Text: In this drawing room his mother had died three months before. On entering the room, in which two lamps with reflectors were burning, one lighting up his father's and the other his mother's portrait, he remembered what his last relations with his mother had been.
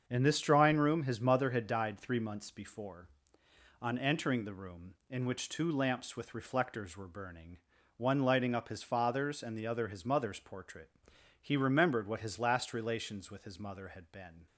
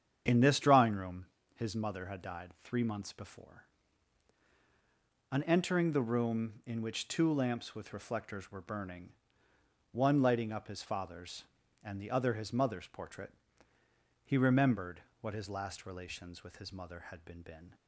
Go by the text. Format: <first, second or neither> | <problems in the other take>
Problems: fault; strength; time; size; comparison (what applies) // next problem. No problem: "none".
first | starts louder than the rest; strong; until 1.2 s; 8 dB; also in the first // pauses between "room" and "his"; slight; at 1.2 s; 0.28 s long // pauses between "died" and "three"; slight; at 2.4 s; 0.16 s long // pauses between "remembered" and "what"; slight; at 14.9 s; 0.22 s long // says "been" twice; at 17.4 s